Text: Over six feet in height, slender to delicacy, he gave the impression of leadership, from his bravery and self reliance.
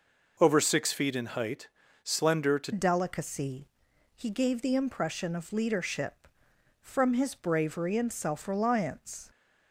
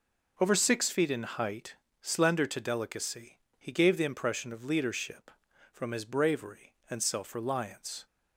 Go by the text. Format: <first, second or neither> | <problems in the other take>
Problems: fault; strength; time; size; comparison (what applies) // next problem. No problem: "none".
second | changes voice at "delicacy"; from 2.7 s on; 6.6 s long